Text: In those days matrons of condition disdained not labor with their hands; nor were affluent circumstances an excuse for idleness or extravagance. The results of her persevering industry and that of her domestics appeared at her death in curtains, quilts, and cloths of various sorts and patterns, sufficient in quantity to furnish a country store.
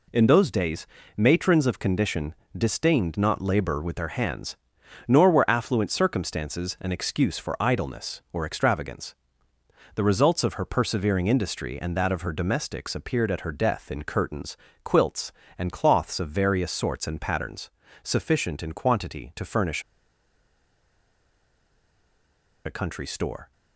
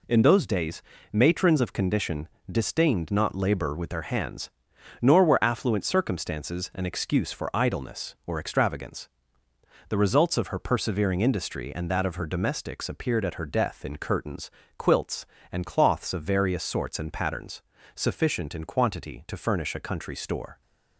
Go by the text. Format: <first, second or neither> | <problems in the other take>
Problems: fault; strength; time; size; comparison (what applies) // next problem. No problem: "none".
second | pauses between "days" and "matrons"; slight; at 0.8 s; 0.30 s long; slight in the second // pauses between "condition" and "disdained"; slight; at 2.3 s; 0.24 s long; slight in the second // pauses between "furnish" and "a"; strong; at 19.8 s; 2.8 s long